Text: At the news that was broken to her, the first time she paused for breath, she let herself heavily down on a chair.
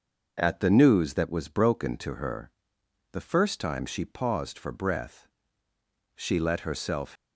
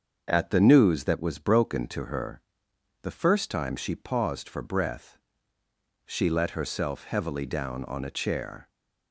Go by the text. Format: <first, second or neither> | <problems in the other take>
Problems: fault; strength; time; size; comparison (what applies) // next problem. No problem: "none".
second | starts louder than the rest; noticeable; until 1.3 s; 6 dB; also in the second // stops before "heavily down on a chair"; at 7.1 s